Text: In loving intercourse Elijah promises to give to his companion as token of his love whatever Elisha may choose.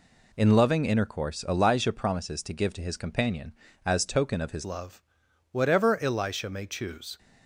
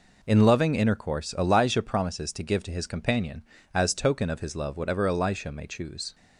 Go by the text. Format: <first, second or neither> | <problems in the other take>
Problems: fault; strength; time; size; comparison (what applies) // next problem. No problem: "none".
second | changes voice at "love"; from 4.6 s on; 2.5 s long // pauses between "love" and "whatever"; noticeable; at 5.0 s; 0.50 s long